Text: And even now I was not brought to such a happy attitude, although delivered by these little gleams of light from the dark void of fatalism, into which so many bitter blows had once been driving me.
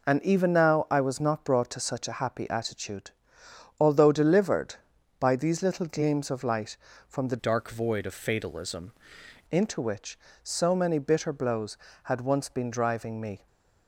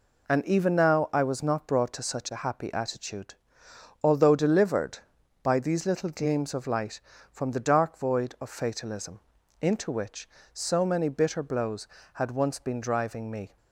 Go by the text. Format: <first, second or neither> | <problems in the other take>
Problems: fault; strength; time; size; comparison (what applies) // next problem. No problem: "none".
second | changes voice from "dark" to "fatalism"; from 7.3 to 8.9 s; 1.6 s long // stays silent after the last word; slight; from 13.3 s on; 0.5 s long